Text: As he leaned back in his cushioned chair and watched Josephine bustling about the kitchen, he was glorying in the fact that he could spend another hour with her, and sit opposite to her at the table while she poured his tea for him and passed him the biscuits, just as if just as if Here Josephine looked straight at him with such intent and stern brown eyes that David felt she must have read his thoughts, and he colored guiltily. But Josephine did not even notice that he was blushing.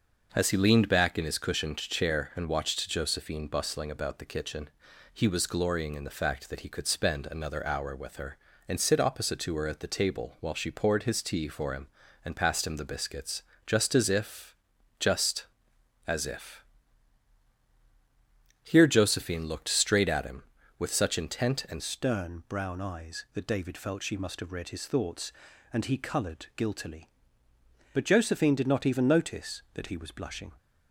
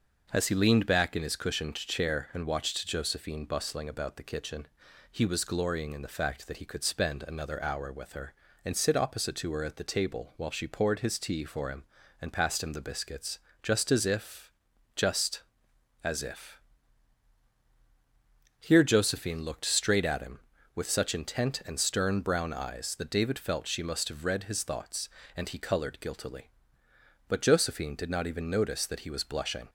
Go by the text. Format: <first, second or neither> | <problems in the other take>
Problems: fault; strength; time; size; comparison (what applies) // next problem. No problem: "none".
second | pauses between "if" and "just"; noticeable; at 14.5 s; 0.46 s long; noticeable in the second // pauses between "if" and "Here"; strong; at 16.6 s; 2.0 s long; strong in the second // changes voice at "stern"; from 21.8 s on; 8.7 s long